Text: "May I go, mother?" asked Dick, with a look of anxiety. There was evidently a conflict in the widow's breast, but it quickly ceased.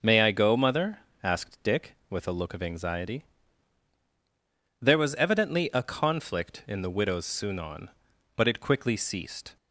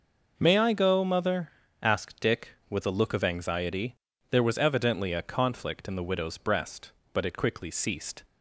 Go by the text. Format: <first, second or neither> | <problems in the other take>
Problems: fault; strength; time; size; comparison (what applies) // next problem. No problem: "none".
second | says "sunon" for "breast"; at 7.2 s